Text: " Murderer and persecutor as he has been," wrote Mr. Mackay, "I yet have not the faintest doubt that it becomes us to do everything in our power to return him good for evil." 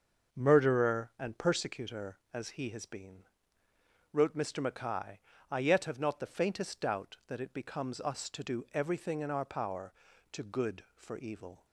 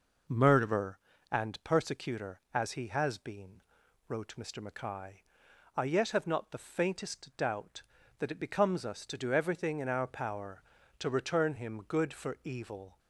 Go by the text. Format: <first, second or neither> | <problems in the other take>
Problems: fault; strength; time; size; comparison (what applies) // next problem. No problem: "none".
second | starts louder than the rest; until 1.4 s; 6.5 dB // skips "return him"; at 10.4 s